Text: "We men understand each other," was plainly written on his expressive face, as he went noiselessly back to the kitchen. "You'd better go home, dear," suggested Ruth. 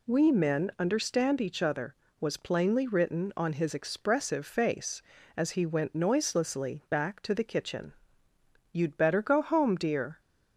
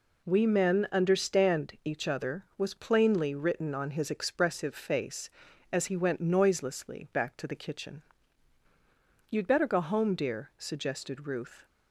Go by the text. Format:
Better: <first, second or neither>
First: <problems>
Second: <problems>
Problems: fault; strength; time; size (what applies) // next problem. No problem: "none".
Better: second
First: stops before "suggested Ruth"; at 10.1 s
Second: none